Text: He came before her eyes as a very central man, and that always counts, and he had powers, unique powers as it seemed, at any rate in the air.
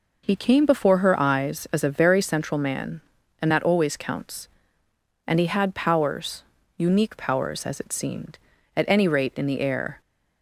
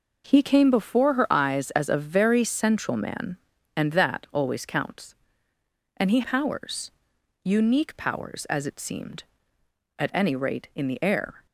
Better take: first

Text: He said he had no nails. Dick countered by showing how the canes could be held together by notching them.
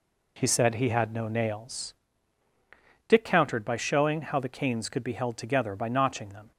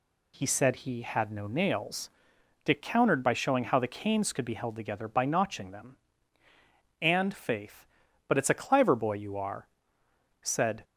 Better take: first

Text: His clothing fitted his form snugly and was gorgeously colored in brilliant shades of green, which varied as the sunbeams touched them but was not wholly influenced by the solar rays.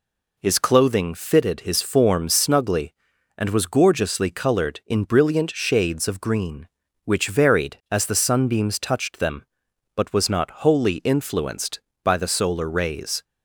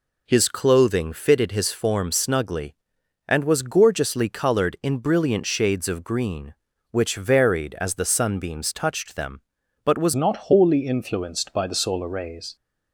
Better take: first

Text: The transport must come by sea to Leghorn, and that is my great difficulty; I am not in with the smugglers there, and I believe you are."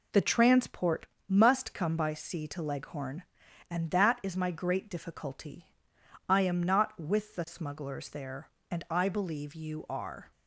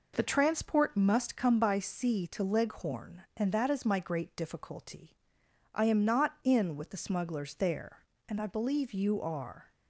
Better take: second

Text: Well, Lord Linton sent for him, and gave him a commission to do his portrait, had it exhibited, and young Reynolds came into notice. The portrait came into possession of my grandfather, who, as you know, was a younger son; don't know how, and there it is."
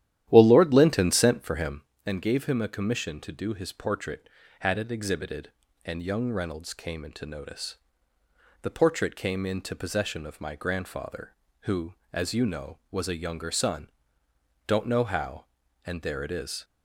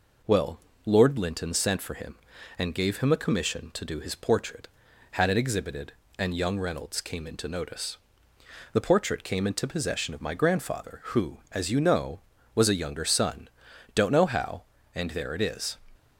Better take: second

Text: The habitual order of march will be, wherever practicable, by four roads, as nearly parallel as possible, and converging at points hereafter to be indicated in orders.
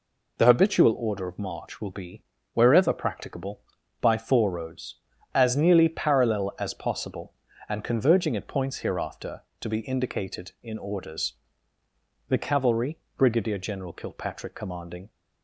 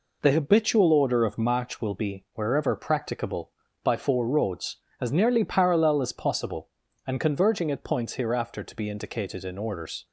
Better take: second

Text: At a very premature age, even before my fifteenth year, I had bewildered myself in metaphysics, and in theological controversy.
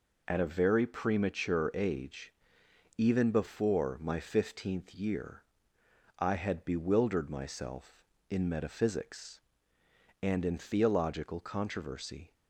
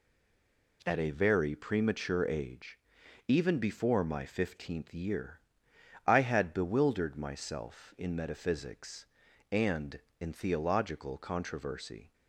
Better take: first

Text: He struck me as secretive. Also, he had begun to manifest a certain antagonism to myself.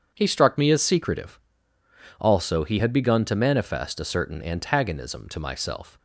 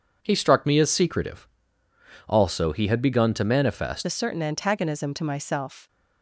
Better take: first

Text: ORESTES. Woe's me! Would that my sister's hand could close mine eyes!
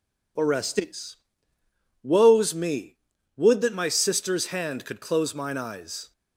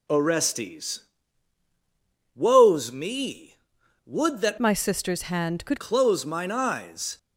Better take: first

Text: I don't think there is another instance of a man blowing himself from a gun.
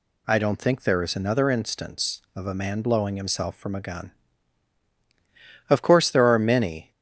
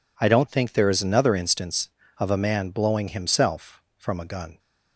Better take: second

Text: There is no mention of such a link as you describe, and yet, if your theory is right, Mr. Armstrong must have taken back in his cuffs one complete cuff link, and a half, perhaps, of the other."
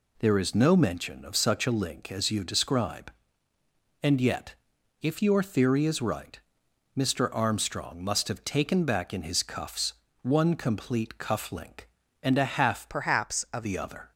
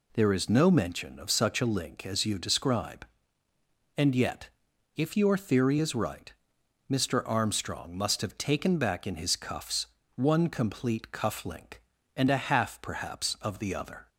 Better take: second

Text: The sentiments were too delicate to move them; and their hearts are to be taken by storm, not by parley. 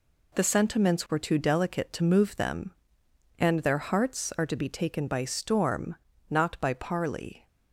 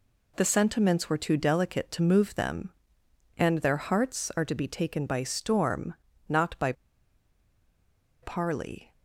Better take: first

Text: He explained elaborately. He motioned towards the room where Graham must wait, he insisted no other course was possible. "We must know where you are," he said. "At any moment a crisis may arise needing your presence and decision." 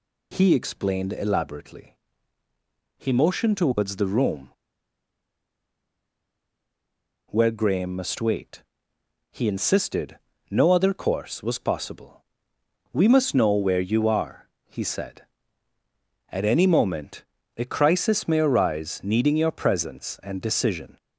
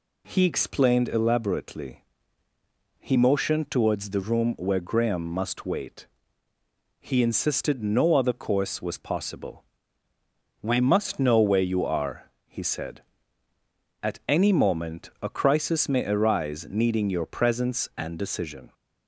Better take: second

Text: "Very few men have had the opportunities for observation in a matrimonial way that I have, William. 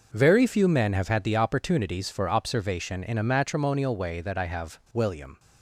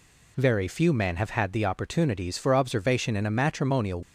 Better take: first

